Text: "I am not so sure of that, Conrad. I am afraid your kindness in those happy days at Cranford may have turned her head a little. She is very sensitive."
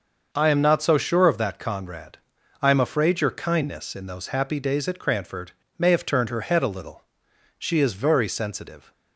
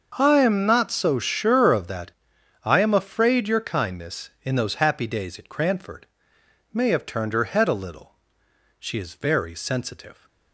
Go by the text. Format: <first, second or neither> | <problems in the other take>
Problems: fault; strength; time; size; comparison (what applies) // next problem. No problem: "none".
first | starts louder than the rest; until 1.2 s; 6.5 dB; noticeable in the first // skips "Conrad"; at 2.3 s // pauses between "Cranford" and "may"; noticeable; at 6.0 s; 0.66 s long; slight in the first